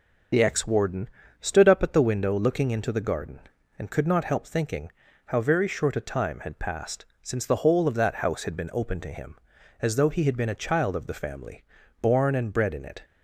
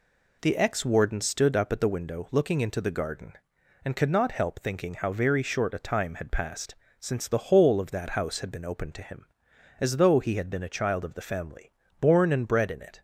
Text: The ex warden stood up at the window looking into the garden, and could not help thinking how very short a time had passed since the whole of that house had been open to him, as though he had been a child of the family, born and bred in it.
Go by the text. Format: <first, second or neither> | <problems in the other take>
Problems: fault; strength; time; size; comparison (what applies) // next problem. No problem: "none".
second | loses the start of "The"; at 0.3 s; 40 ms // pauses between "warden" and "stood"; slight; at 1.0 s; 0.32 s long // pauses between "thinking" and "how"; slight; at 4.9 s; 0.36 s long // pauses between "passed" and "since"; slight; at 7.0 s; 0.16 s long; slight in the second